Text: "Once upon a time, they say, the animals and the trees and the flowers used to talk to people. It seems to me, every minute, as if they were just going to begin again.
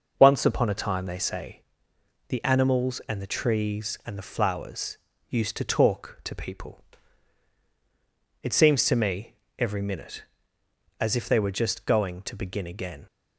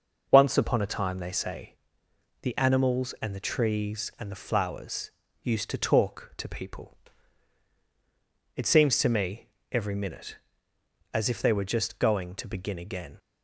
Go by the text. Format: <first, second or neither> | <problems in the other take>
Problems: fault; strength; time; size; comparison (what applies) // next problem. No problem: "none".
neither | pauses between "flowers" and "used"; slight; the same in both